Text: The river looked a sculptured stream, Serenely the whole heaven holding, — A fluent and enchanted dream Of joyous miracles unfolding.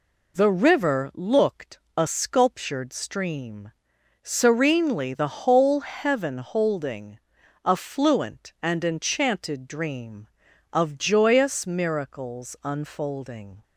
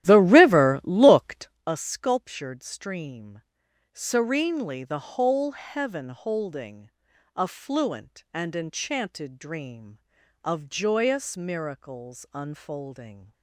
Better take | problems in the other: first | starts louder than the rest; strong; until 1.6 s; 12.5 dB // pauses between "looked" and "a"; slight; at 1.4 s; 0.16 s long; slight in the first

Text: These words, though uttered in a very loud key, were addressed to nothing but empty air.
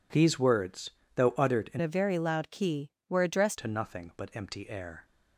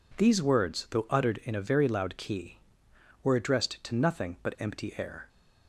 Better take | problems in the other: second | changes voice from "a" to "addressed"; from 1.8 to 3.5 s; 1.7 s long

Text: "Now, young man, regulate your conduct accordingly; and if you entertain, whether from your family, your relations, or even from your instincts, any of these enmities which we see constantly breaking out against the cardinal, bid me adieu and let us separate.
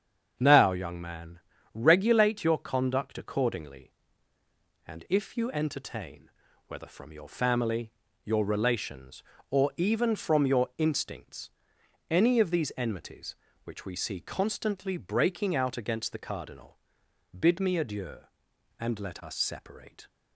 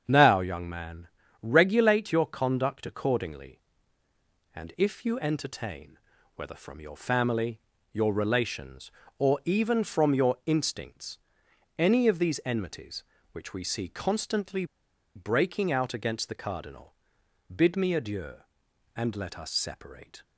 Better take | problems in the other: first | starts louder than the rest; strong; until 1.0 s; 7.5 dB; strong in the first // pauses between "constantly" and "breaking"; noticeable; at 14.6 s; 0.50 s long

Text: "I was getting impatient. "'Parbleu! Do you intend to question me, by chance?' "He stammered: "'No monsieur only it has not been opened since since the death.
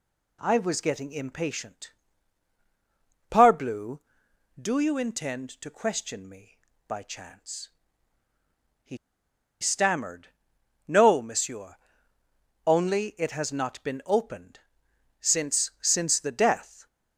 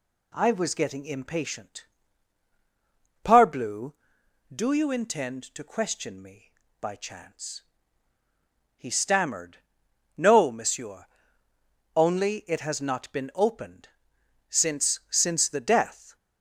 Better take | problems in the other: second | pauses between "He" and "stammered"; noticeable; at 8.9 s; 0.65 s long // pauses between "monsieur" and "only"; noticeable; at 11.7 s; 0.90 s long; noticeable in the second // pauses between "opened" and "since"; noticeable; at 14.6 s; 0.58 s long; noticeable in the second

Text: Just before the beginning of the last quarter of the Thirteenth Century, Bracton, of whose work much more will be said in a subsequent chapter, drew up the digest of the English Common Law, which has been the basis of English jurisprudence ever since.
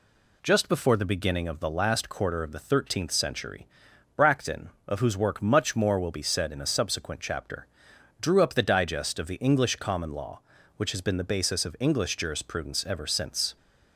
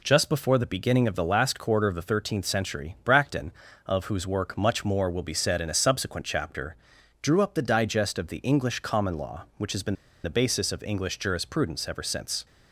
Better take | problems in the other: first | pauses between "been" and "the"; slight; at 9.9 s; 0.29 s long

